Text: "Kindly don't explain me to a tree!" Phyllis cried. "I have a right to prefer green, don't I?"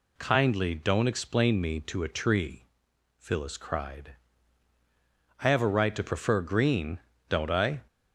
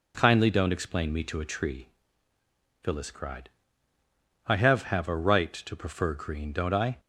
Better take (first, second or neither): first